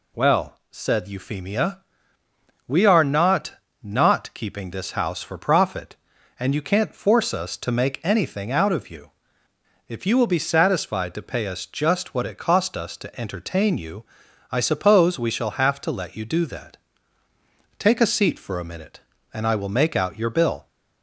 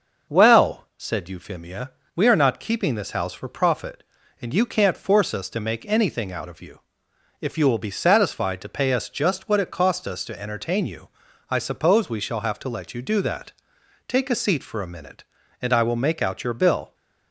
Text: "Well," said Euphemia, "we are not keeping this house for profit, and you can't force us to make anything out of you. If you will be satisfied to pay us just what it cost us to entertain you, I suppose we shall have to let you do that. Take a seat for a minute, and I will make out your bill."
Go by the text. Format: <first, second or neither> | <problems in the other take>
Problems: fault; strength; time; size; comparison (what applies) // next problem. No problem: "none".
second | says "not" twice; at 3.8 s